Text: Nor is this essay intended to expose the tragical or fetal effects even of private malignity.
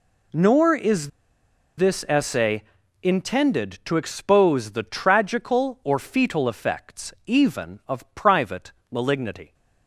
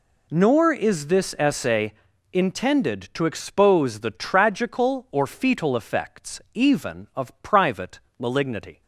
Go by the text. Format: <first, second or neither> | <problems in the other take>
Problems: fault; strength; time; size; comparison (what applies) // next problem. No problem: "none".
second | pauses between "is" and "this"; noticeable; at 1.0 s; 0.69 s long // pauses between "essay" and "intended"; at 2.6 s; 0.40 s long; also in the second // pauses between "private" and "malignity"; slight; at 8.7 s; 0.18 s long; slight in the second